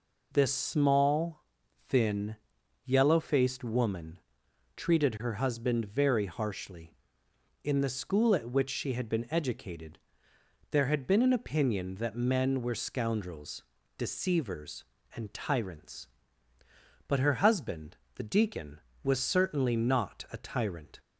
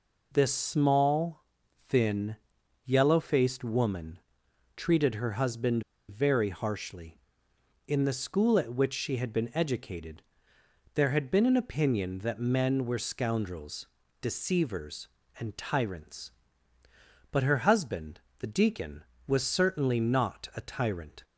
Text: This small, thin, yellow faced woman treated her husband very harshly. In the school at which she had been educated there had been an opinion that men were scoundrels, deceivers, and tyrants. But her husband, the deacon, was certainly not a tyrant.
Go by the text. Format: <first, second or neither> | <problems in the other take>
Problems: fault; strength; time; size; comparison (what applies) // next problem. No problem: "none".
first | pauses between "woman" and "treated"; noticeable; at 4.1 s; 0.58 s long; noticeable in the first // pauses between "husband" and "very"; slight; at 5.8 s; 0.26 s long // pauses between "educated" and "there"; noticeable; at 10.2 s; 0.74 s long; noticeable in the first